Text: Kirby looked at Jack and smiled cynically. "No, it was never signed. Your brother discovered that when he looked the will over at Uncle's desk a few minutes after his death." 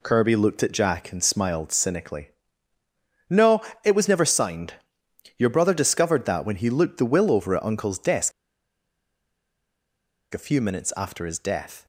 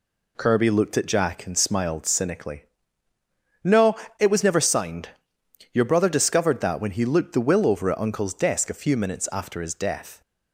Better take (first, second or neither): second